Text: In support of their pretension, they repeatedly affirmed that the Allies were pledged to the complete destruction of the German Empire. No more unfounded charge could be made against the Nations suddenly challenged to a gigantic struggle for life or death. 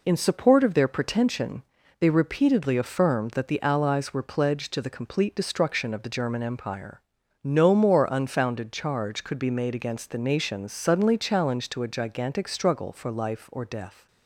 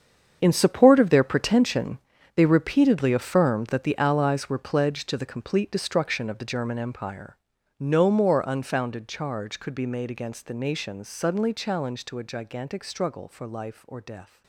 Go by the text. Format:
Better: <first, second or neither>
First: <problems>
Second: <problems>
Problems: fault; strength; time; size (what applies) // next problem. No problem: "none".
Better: first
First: none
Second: gets quieter; strong; throughout; 13.5 dB